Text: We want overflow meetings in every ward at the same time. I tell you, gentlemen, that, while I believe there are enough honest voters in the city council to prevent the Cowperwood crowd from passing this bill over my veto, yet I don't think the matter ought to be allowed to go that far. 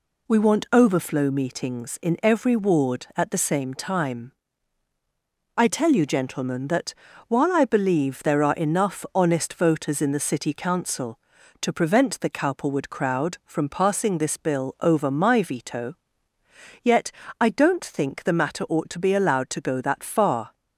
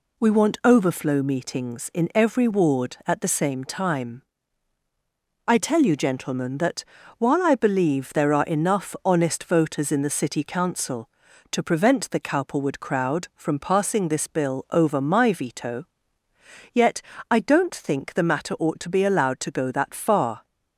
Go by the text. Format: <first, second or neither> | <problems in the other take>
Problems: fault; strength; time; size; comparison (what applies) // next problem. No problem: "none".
neither | pauses between "yet" and "I"; slight; the same in both